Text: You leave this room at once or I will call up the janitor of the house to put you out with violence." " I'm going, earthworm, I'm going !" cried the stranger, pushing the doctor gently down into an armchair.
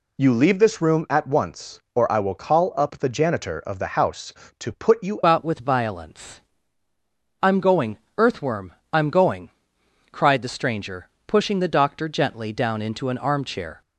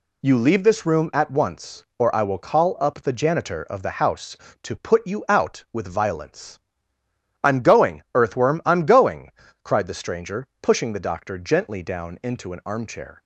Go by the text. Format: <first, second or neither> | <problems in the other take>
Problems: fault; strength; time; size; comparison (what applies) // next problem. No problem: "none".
second | changes voice at "out"; from 5.2 s on; 8.6 s long